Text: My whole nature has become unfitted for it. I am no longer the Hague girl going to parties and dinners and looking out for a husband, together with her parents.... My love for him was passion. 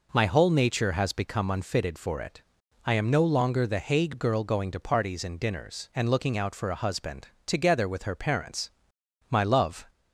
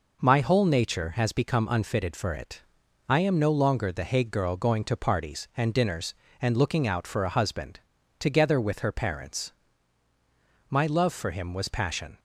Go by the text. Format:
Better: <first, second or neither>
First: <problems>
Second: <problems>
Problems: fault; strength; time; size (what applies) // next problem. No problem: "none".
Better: second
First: stops before "for him was passion"; at 9.8 s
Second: none